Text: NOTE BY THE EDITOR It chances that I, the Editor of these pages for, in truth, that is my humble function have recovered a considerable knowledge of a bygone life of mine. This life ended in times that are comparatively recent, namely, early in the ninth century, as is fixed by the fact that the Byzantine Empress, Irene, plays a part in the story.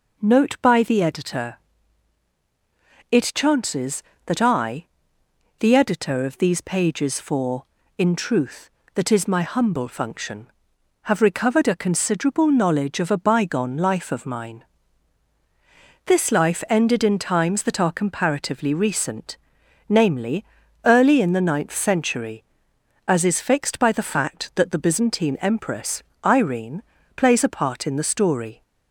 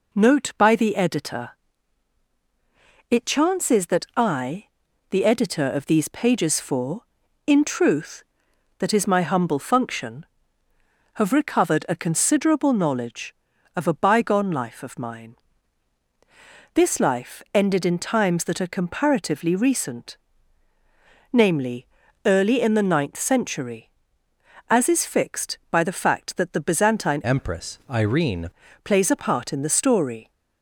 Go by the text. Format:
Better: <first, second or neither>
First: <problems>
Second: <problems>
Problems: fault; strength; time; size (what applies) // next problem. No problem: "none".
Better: first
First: pauses between "EDITOR" and "It"; strong; at 1.5 s; 1.5 s long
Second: pauses between "EDITOR" and "It"; strong; at 1.4 s; 1.6 s long // changes voice from "Empress" to "Irene"; from 27.2 to 28.4 s; 1.2 s long